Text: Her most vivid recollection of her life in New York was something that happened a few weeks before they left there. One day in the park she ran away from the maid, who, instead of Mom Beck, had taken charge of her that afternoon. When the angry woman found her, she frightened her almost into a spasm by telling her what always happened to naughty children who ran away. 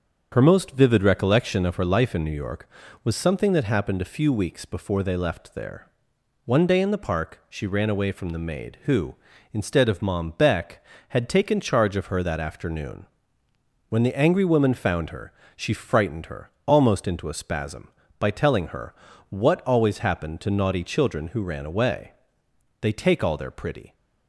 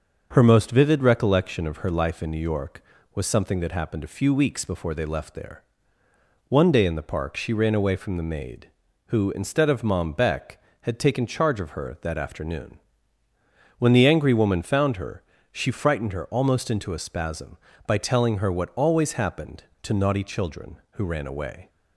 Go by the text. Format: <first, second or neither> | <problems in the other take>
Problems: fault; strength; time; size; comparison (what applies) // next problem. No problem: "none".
second | starts louder than the rest; until 1.3 s; 7 dB; also in the second // pauses between "her" and "almost"; slight; at 16.4 s; 0.16 s long // pauses between "her" and "what"; slight; at 18.9 s; 0.34 s long // goes on to say "They take all their pretty"; noticeable; from 22.7 s on; 1.1 s long